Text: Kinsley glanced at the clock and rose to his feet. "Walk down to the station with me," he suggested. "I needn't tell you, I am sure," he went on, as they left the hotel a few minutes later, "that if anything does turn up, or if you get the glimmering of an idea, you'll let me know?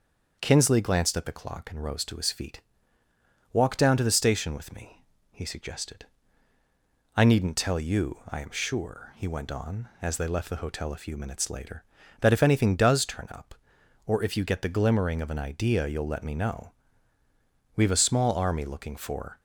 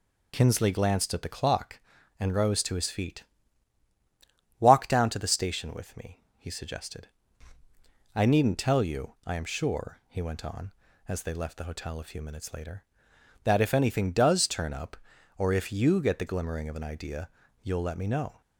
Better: second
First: starts louder than the rest; until 1.4 s; 6.5 dB // goes on to say "We've a small army looking for"; from 17.7 s on; 1.6 s long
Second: none

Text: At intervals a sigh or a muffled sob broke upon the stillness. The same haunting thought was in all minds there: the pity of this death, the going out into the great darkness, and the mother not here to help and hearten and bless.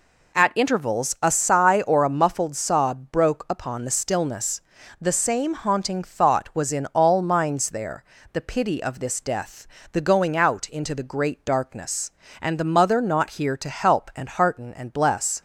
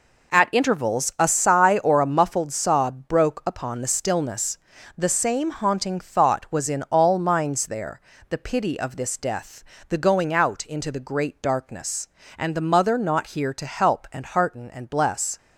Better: first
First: none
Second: gets quieter; strong; throughout; 8.5 dB

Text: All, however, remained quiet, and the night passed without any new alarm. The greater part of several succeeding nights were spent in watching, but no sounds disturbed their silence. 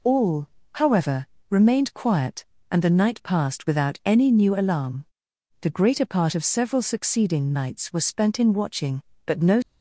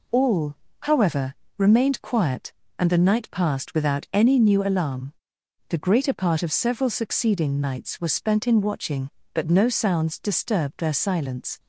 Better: second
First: stops before "sounds disturbed their silence"; at 9.6 s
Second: none

